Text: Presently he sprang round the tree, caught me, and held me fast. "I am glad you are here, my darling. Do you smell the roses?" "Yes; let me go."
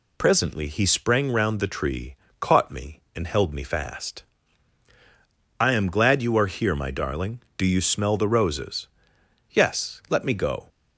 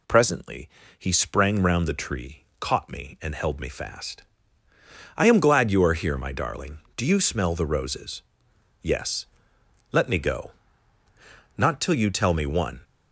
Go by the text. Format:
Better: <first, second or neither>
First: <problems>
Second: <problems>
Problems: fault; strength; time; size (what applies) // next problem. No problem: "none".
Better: first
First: none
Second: pauses between "Presently" and "he"; slight; at 0.6 s; 0.30 s long // goes on to say "Not till you tell me one"; noticeable; from 11.5 s on; 1.2 s long